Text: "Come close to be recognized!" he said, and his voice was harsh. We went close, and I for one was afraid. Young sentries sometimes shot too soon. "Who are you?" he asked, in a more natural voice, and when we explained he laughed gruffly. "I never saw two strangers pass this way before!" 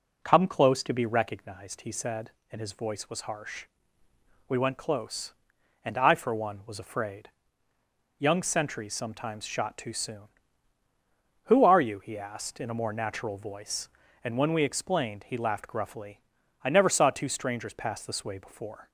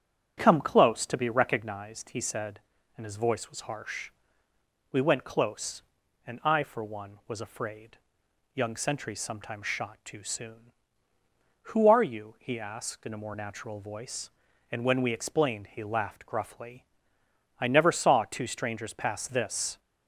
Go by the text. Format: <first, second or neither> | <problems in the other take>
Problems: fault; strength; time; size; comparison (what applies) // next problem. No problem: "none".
first | starts louder than the rest; strong; until 1.4 s; 9 dB // stops before "way before"; at 19.7 s